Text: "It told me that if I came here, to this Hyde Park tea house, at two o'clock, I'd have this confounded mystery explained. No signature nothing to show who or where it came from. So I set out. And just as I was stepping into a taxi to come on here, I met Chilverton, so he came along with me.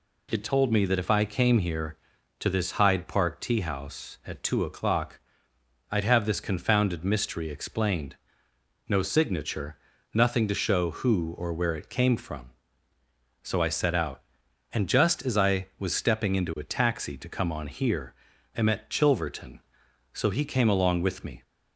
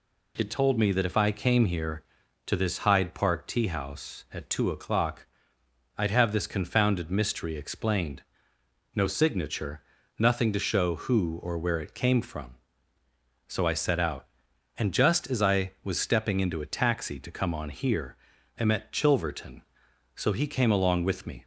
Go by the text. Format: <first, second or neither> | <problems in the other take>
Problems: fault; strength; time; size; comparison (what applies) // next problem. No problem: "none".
neither | pauses between "signature" and "nothing"; the same in both